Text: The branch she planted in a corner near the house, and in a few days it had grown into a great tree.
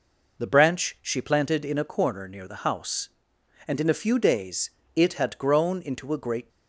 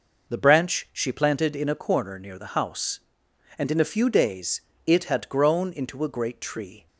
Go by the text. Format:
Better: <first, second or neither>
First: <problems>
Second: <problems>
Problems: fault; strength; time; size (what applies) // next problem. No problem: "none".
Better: second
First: pauses between "days" and "it"; slight; at 4.7 s; 0.26 s long // stops before "tree"; at 6.5 s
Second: pauses between "days" and "it"; slight; at 4.6 s; 0.26 s long